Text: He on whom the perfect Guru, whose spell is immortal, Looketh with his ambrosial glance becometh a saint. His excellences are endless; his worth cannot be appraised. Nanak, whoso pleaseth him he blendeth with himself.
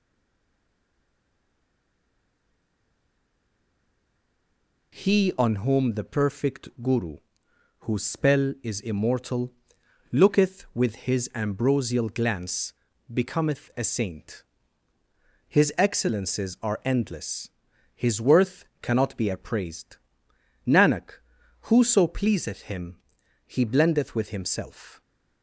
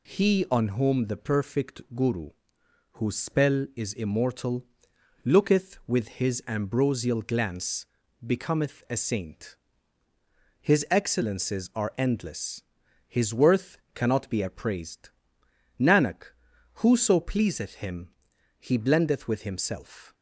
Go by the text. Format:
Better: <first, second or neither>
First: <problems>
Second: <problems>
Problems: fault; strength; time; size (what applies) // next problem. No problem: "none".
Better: second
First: stays silent before the first word; strong; until 4.9 s; 4.9 s long // pauses between "perfect" and "Guru"; slight; at 6.6 s; 0.16 s long // pauses between "glance" and "becometh"; at 12.7 s; 0.38 s long // pauses between "worth" and "cannot"; slight; at 18.6 s; 0.16 s long // pauses between "him" and "he"; noticeable; at 22.9 s; 0.50 s long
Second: pauses between "perfect" and "Guru"; slight; at 1.8 s; 0.16 s long // pauses between "glance" and "becometh"; at 7.8 s; 0.38 s long // pauses between "worth" and "cannot"; slight; at 13.7 s; 0.16 s long // pauses between "him" and "he"; noticeable; at 18.1 s; 0.50 s long